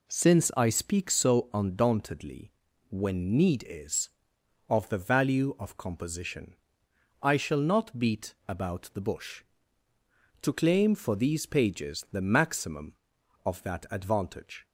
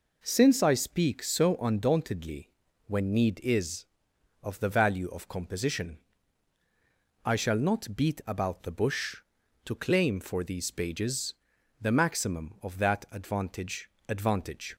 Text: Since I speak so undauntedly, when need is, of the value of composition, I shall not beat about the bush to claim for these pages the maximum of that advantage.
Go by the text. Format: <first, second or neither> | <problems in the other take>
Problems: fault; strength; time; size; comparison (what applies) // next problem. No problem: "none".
first | pauses between "pages" and "the"; noticeable; at 11.3 s; 0.48 s long // says "advantage" twice; at 14.0 s